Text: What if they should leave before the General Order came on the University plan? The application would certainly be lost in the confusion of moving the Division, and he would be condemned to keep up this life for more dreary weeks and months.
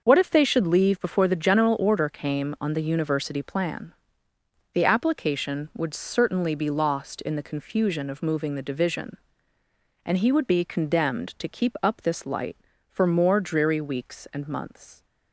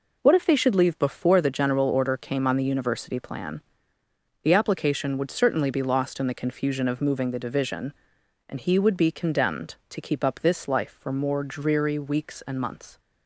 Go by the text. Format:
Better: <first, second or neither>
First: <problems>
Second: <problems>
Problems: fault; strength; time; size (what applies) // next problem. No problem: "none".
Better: second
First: says "light" for "life"; at 12.2 s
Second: none